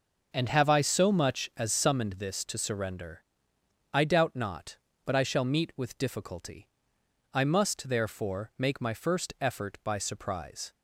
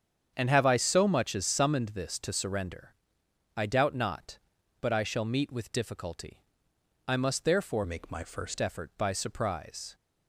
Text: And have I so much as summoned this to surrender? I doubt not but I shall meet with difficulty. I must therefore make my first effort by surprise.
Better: first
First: none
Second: starts louder than the rest; strong; until 1.3 s; 7.5 dB // changes voice from "make" to "first"; from 7.8 to 8.5 s; 0.7 s long

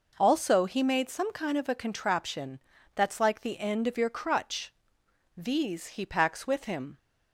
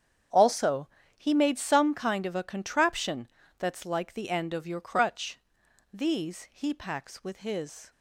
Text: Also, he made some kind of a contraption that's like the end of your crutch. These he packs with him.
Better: first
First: pauses between "contraption" and "that's"; slight; at 2.5 s; 0.34 s long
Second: starts louder than the rest; strong; until 1.6 s; 8 dB // pauses between "contraption" and "that's"; slight; at 3.2 s; 0.30 s long // says "his" for "him"; at 7.3 s

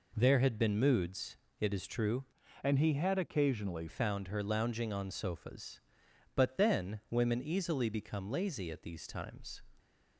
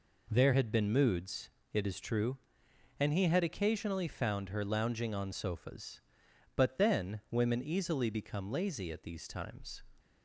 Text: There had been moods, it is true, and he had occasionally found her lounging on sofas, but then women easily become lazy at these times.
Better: second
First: changes voice from "and" to "occasionally"; from 2.6 to 3.8 s; 1.2 s long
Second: none

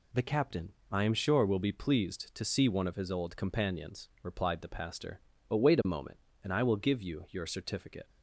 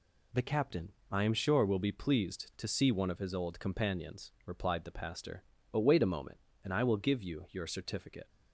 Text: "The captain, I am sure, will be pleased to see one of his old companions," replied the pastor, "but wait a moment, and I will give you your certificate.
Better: neither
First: none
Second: none

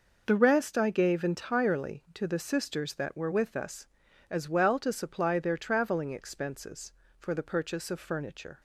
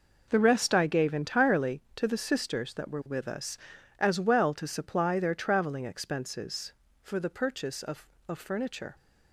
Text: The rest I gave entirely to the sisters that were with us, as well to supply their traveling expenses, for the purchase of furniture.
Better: first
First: none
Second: says "of" twice; at 8.2 s

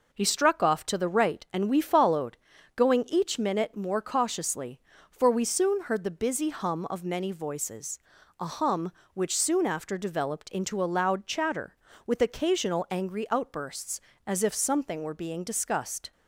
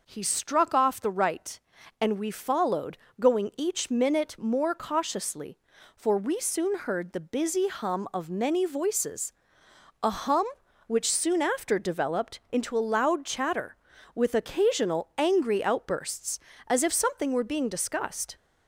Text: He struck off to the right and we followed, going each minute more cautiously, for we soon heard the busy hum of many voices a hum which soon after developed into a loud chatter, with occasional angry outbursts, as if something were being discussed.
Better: first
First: pauses between "voices" and "a"; at 7.9 s; 0.42 s long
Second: skips "to"; at 0.9 s // pauses between "voices" and "a"; noticeable; at 9.3 s; 0.68 s long

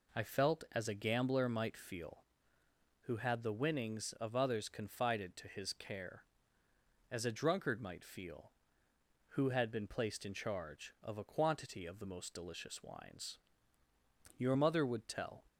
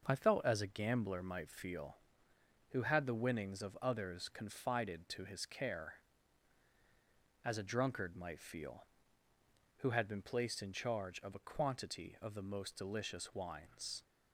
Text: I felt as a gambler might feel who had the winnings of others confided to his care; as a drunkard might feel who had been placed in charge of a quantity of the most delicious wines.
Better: second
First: goes on to say "Your mother would tell"; noticeable; from 14.3 s on; 1.0 s long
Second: none

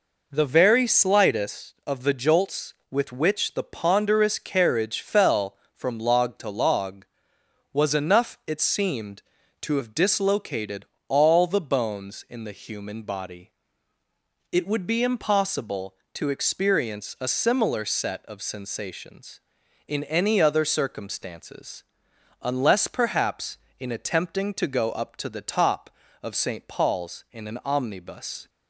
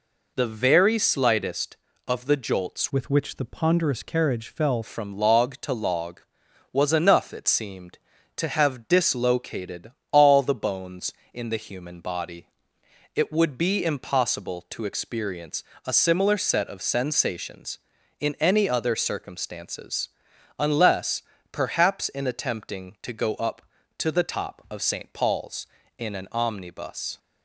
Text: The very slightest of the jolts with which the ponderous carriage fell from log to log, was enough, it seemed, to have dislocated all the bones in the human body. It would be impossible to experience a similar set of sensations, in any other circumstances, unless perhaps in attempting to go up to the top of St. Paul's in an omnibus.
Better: first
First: pauses between "dislocated" and "all"; slight; at 10.8 s; 0.22 s long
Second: changes voice from "with" to "fell"; from 2.9 to 4.8 s; 1.9 s long // pauses between "dislocated" and "all"; slight; at 9.9 s; 0.18 s long // pauses between "experience" and "a"; slight; at 15.6 s; 0.24 s long // pauses between "unless" and "perhaps"; slight; at 21.2 s; 0.30 s long

